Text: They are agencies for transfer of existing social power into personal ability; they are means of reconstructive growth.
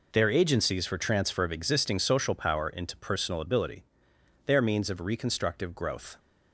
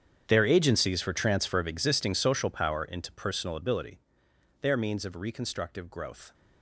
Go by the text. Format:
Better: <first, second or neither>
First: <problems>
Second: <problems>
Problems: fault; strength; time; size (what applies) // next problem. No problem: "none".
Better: first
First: none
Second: gets quieter; strong; throughout; 19 dB